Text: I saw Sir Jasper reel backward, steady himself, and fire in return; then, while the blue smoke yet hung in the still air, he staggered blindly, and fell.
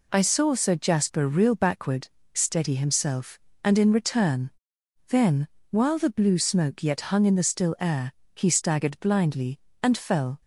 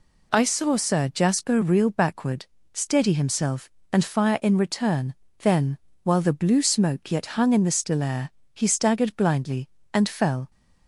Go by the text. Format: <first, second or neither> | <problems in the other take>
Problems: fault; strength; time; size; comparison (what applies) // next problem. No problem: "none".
second | skips "fire"; at 3.7 s